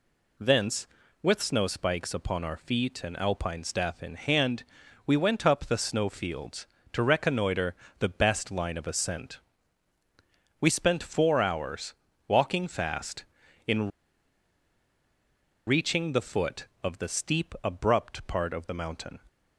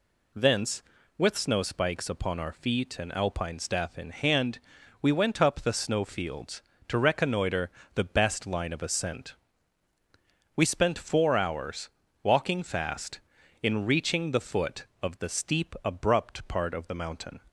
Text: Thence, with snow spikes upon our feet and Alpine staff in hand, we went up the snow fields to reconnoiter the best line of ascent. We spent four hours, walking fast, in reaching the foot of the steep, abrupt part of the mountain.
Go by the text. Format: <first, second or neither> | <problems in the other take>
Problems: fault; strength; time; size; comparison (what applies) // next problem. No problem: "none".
second | pauses between "reconnoiter" and "the"; slight; at 7.7 s; 0.26 s long; slight in the second // pauses between "in" and "reaching"; strong; at 13.8 s; 1.7 s long